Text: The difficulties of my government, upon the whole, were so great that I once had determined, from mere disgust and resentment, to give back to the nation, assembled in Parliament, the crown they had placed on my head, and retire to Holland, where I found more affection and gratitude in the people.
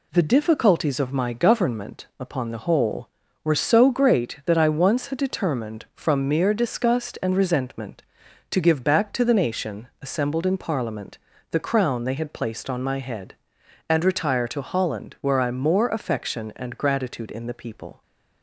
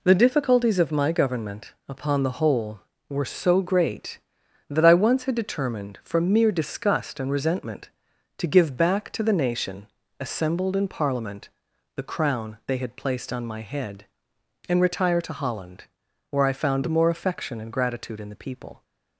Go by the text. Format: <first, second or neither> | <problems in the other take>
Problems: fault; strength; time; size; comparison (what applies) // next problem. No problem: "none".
second | skips "found"; at 15.5 s